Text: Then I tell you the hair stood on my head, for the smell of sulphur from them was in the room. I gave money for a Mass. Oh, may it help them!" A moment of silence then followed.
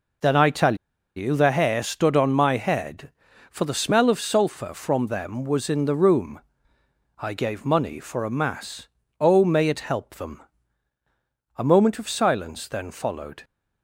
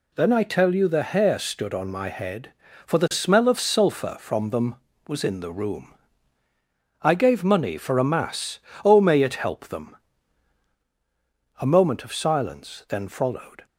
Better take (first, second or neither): second